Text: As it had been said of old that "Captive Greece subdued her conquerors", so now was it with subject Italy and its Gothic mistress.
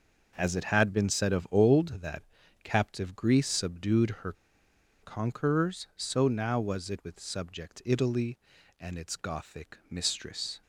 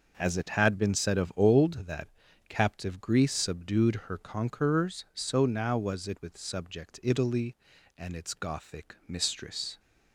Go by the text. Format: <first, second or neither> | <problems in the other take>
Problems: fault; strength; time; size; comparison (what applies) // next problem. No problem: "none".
second | pauses between "that" and "Captive"; at 2.2 s; 0.40 s long; also in the second // pauses between "her" and "conquerors"; noticeable; at 4.3 s; 0.70 s long